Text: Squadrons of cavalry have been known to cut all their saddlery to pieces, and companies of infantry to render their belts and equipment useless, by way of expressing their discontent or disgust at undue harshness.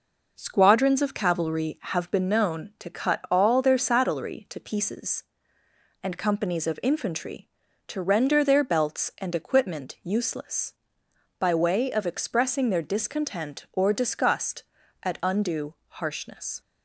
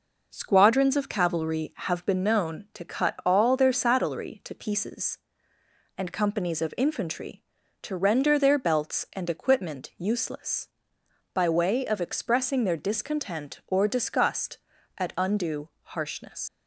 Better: first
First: pauses between "undue" and "harshness"; slight; at 15.7 s; 0.16 s long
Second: pauses between "undue" and "harshness"; slight; at 15.6 s; 0.16 s long // leaves "harshness" unfinished; at 16.4 s; 70 ms

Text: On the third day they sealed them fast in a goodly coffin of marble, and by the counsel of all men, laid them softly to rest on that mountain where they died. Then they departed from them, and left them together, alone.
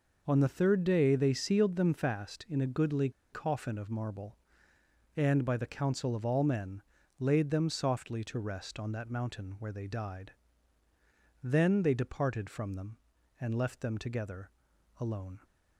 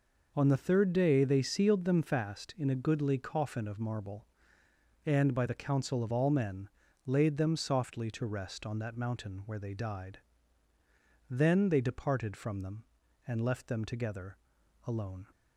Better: second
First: pauses between "goodly" and "coffin"; slight; at 3.0 s; 0.22 s long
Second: none

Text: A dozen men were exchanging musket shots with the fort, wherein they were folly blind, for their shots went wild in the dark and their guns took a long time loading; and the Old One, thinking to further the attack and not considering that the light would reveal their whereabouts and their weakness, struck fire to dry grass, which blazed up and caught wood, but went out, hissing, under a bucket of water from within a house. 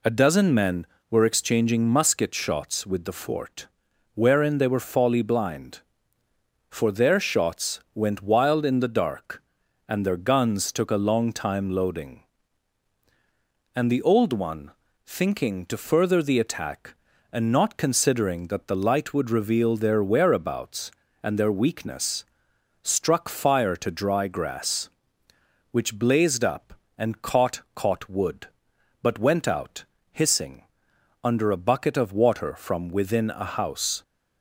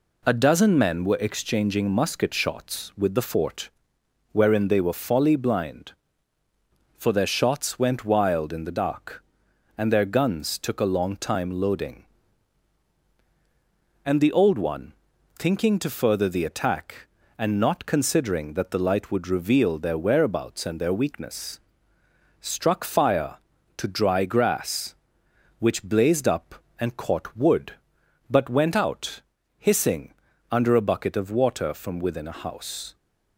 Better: second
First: says "caught" twice; at 27.7 s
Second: none

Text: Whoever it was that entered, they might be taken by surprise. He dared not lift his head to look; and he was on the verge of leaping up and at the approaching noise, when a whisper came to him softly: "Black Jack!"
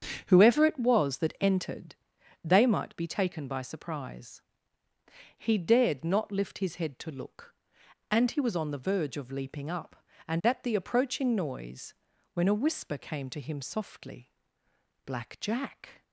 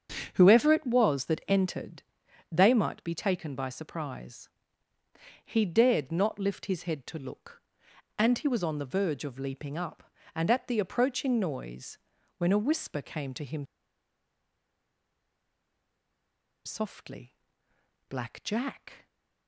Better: first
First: starts louder than the rest; strong; until 1.2 s; 7.5 dB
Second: starts louder than the rest; strong; until 1.3 s; 7.5 dB // pauses between "him" and "softly"; strong; at 13.6 s; 3.0 s long

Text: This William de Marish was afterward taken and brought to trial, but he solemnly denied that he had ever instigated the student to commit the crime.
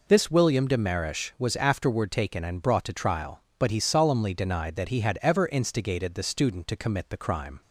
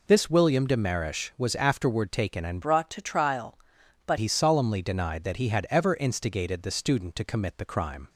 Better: first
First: none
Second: changes voice from "brought" to "but"; from 2.6 to 4.1 s; 1.5 s long

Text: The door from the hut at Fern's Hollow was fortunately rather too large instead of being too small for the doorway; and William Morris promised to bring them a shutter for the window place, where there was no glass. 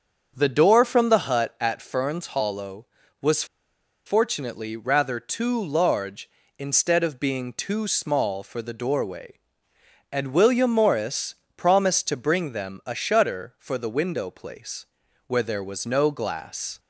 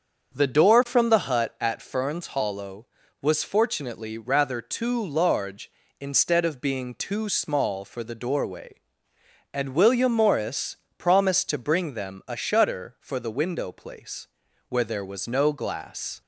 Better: second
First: starts louder than the rest; until 1.3 s; 7 dB // pauses between "was" and "fortunately"; noticeable; at 3.4 s; 0.61 s long // pauses between "Morris" and "promised"; slight; at 11.3 s; 0.24 s long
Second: starts louder than the rest; until 1.3 s; 7 dB // pauses between "Morris" and "promised"; slight; at 10.7 s; 0.24 s long

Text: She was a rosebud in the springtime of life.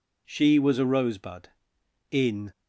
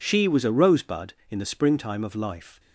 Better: second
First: stops before "the springtime of life"; at 2.5 s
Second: none

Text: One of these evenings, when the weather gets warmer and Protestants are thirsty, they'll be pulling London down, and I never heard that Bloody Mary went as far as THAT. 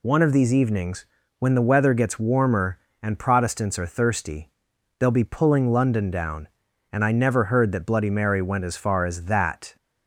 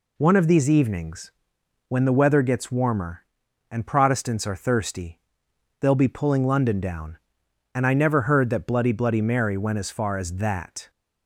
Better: first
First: none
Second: says "Bloody" twice; at 8.9 s

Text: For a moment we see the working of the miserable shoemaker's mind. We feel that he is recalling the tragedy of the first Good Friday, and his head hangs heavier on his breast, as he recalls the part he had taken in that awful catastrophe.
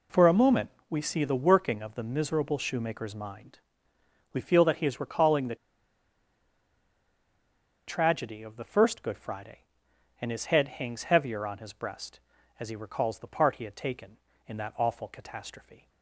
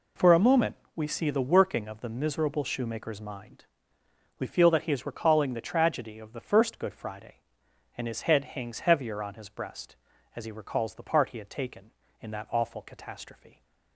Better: second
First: pauses between "moment" and "we"; slight; at 0.7 s; 0.18 s long // pauses between "the" and "tragedy"; strong; at 5.5 s; 2.3 s long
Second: pauses between "moment" and "we"; slight; at 0.7 s; 0.18 s long

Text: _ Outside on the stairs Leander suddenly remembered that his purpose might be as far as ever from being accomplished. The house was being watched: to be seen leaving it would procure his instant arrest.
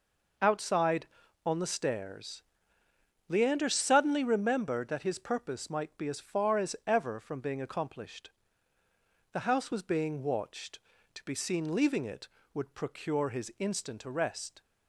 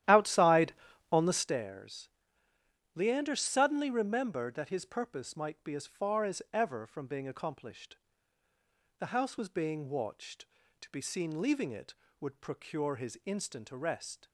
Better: first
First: pauses between "stairs" and "Leander"; noticeable; at 2.4 s; 0.86 s long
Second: starts louder than the rest; strong; until 1.6 s; 12.5 dB // pauses between "stairs" and "Leander"; noticeable; at 2.0 s; 0.86 s long

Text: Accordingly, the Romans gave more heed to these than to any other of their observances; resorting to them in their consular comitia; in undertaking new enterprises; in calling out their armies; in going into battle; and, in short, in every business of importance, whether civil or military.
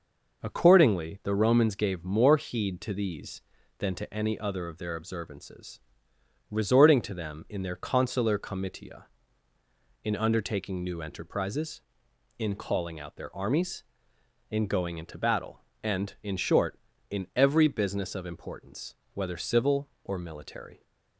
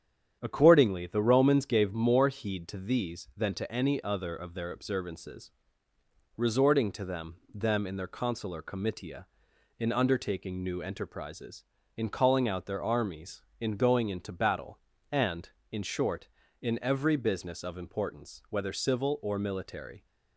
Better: first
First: none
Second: starts louder than the rest; strong; until 1.4 s; 8.5 dB // says "them" twice; at 7.5 s

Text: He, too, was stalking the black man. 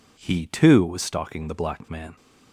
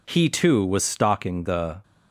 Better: first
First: none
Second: stops before "black man"; at 1.8 s

